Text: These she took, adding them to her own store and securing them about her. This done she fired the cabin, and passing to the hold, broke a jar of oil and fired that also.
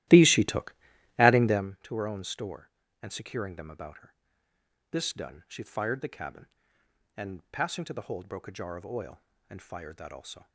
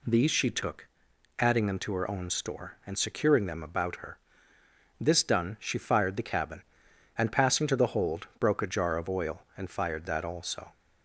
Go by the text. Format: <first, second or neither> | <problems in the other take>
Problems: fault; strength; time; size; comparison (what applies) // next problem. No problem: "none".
second | starts louder than the rest; strong; until 1.7 s; 15.5 dB